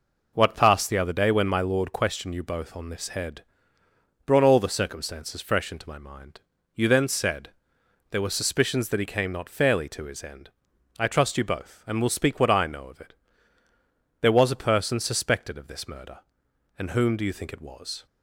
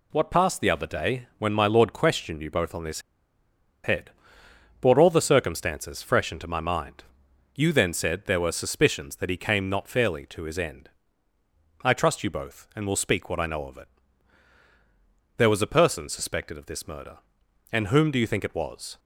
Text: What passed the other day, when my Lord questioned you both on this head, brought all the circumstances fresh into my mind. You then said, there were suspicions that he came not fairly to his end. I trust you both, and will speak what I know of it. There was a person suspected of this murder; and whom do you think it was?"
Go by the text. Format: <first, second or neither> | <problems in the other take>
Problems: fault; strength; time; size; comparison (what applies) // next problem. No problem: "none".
first | pauses between "this" and "head"; noticeable; at 3.0 s; 0.83 s long